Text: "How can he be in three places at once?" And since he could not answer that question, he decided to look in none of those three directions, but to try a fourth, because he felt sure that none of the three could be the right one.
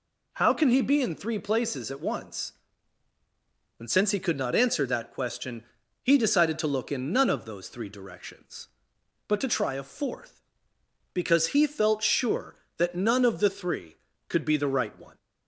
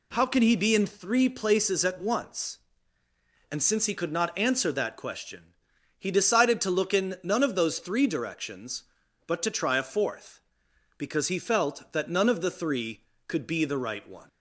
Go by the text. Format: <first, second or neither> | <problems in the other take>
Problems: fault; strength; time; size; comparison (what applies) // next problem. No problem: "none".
first | skips "sure"; at 11.9 s